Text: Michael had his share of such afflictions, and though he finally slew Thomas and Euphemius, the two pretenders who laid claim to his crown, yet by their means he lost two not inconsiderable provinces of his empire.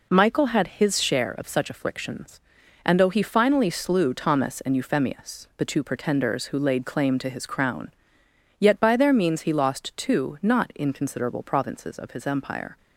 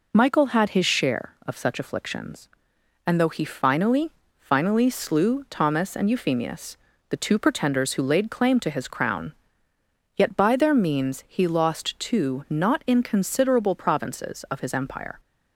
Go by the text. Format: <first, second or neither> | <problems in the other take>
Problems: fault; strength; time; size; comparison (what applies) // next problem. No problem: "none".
first | says "finally" twice; at 4.3 s